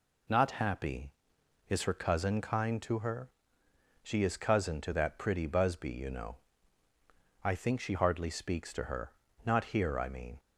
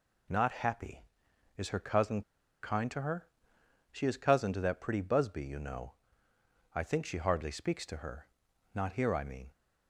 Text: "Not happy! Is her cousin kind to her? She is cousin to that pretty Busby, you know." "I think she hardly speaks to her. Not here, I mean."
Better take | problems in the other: first | pauses between "cousin" and "kind"; at 2.2 s; 0.41 s long

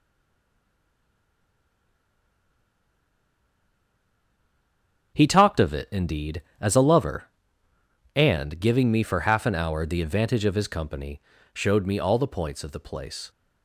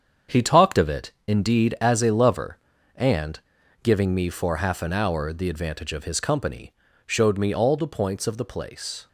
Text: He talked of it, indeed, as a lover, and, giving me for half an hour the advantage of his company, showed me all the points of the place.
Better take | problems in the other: second | stays silent before the first word; strong; until 5.1 s; 5.1 s long // starts louder than the rest; strong; until 6.1 s; 7 dB; strong in the second

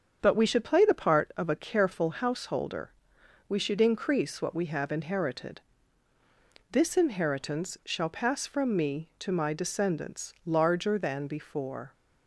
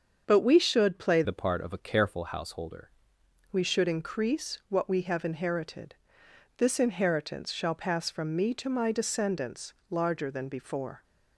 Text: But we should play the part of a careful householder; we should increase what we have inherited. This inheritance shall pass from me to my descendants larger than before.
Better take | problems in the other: first | starts louder than the rest; until 1.2 s; 7 dB; strong in the first // changes voice from "the" to "householder"; from 1.2 to 2.8 s; 1.6 s long // pauses between "descendants" and "larger"; slight; at 9.7 s; 0.18 s long

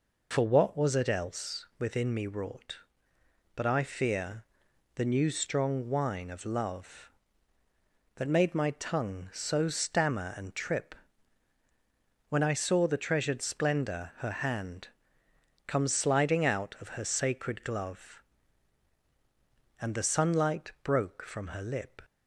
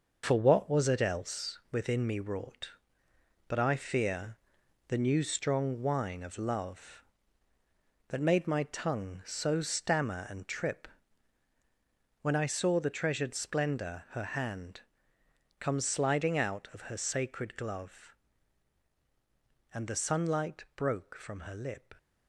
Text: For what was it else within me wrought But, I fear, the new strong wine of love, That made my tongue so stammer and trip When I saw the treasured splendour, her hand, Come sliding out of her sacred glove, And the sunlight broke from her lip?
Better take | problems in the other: first | gets quieter; throughout; 6 dB // pauses between "trip" and "When"; strong; at 10.8 s; 1.3 s long; strong in the first

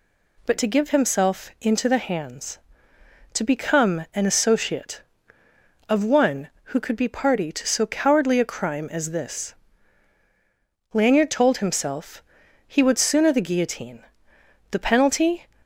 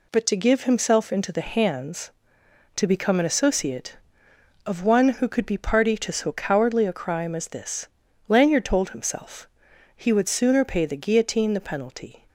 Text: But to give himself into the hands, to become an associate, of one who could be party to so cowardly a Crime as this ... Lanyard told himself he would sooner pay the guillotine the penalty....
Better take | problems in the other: second | pauses between "himself" and "he"; at 12.2 s; 0.44 s long; noticeable in the second // skips "pay"; at 13.3 s // pauses between "guillotine" and "the"; noticeable; at 14.0 s; 0.68 s long

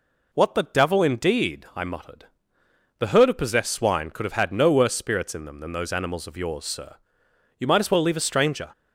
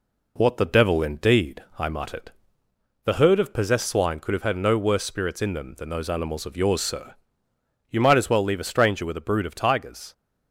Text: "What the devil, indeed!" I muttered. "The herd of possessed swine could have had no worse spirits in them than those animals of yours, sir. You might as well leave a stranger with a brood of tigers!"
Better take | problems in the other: second | stops before "with a brood of tigers"; at 8.7 s

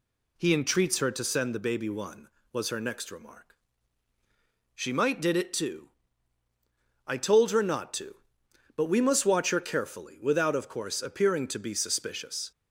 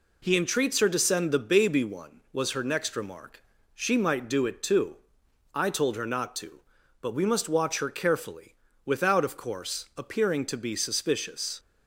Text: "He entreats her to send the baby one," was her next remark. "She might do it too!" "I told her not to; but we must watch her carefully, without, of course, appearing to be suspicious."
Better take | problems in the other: second | says "did" for "do"; at 5.1 s

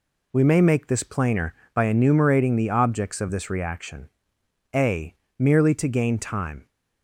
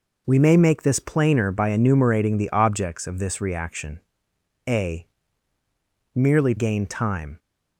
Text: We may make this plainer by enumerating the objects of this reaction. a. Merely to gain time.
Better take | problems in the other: first | skips "to"; at 6.5 s

